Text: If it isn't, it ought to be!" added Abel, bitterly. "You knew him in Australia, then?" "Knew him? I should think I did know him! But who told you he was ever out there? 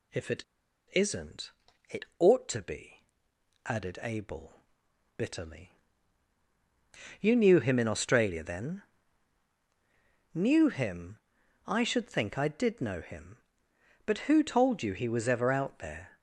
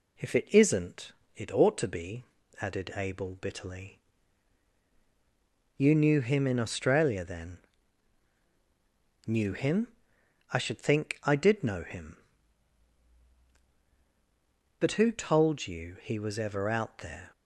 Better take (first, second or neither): second